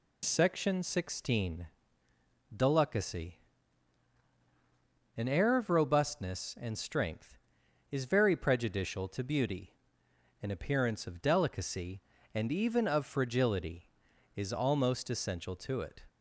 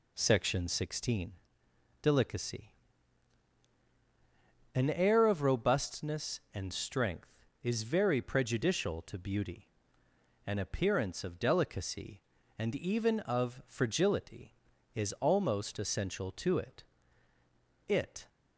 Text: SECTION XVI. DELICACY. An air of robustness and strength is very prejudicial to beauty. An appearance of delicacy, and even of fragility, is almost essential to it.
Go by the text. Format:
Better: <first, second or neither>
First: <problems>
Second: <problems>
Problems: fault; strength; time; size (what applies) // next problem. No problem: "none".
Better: first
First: none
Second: says "it" twice; at 17.8 s